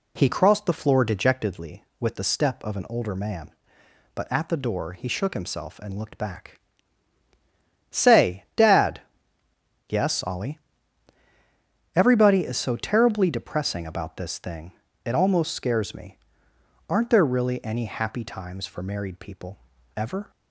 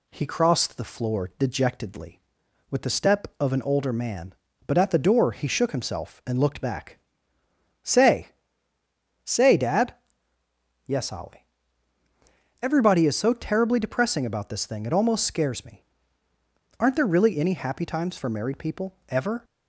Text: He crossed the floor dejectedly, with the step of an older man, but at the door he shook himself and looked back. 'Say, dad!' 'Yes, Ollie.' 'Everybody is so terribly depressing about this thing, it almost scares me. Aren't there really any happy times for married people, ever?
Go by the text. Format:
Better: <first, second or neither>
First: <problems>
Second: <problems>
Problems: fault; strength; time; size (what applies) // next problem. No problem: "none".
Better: first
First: none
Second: says "Say" twice; at 9.2 s